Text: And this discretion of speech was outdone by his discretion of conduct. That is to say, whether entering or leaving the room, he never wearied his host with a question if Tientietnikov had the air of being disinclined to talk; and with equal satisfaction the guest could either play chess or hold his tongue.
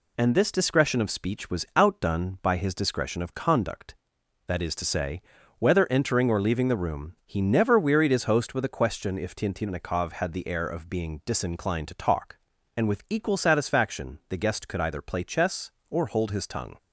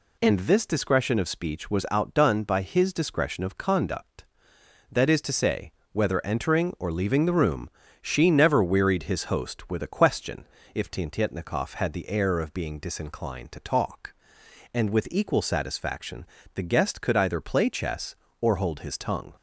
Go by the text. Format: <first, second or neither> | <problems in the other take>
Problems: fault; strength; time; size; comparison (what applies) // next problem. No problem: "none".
first | says "she" for "he"; at 8.0 s // pauses between "question" and "if"; slight; at 10.4 s; 0.26 s long // pauses between "satisfaction" and "the"; slight; at 16.2 s; 0.30 s long